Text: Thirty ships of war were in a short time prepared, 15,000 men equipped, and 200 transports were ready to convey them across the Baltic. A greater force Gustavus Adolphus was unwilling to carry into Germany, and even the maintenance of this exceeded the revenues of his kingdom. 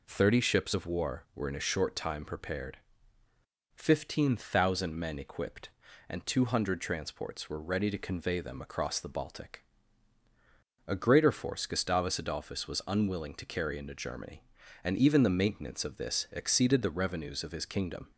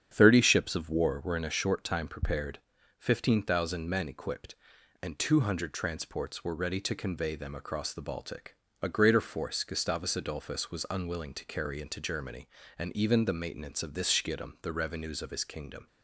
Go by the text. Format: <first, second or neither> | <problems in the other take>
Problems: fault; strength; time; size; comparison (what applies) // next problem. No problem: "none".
first | starts louder than the rest; strong; until 1.1 s; 8.5 dB // says "schiedam" for "exceeded"; at 14.0 s